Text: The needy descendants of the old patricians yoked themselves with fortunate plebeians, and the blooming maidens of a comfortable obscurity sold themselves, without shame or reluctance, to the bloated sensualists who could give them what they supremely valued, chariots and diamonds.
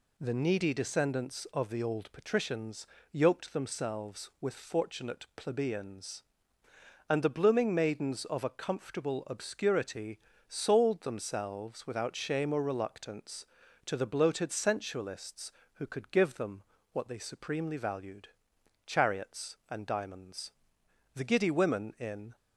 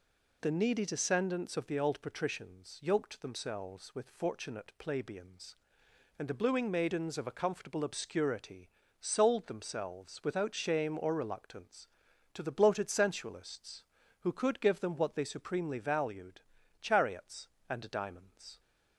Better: second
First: pauses between "patricians" and "yoked"; slight; at 2.8 s; 0.24 s long // pauses between "obscurity" and "sold"; slight; at 10.1 s; 0.28 s long // pauses between "them" and "what"; slight; at 16.6 s; 0.30 s long // goes on to say "The giddy women in"; noticeable; from 21.1 s on; 1.2 s long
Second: pauses between "obscurity" and "sold"; slight; at 8.6 s; 0.32 s long

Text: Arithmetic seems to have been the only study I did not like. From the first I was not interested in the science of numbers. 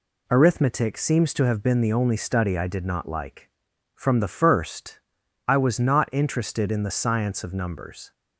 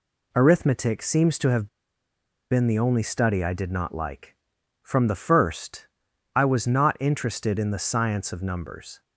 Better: first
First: pauses between "first" and "I"; noticeable; at 5.0 s; 0.46 s long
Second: pauses between "have" and "been"; noticeable; at 1.6 s; 0.83 s long // pauses between "first" and "I"; noticeable; at 5.8 s; 0.46 s long

